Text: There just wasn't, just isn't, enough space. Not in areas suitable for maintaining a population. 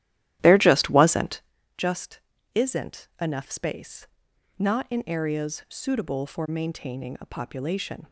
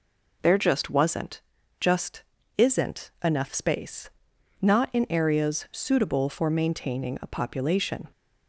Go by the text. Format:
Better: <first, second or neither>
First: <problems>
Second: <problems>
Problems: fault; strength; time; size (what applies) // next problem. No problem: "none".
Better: second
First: starts louder than the rest; strong; until 1.6 s; 13.5 dB // pauses between "just" and "isn't"; slight; at 2.1 s; 0.34 s long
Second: pauses between "just" and "isn't"; slight; at 2.2 s; 0.34 s long